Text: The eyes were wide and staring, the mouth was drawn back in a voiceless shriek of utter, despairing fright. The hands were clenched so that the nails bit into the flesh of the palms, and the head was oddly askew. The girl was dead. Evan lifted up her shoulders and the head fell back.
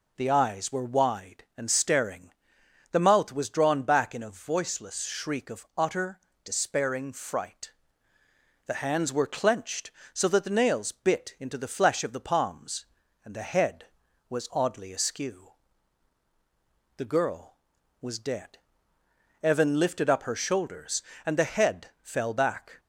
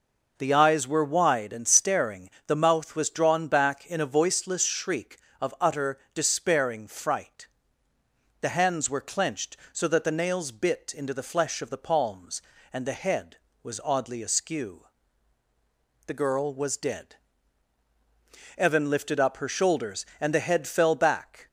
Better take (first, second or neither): neither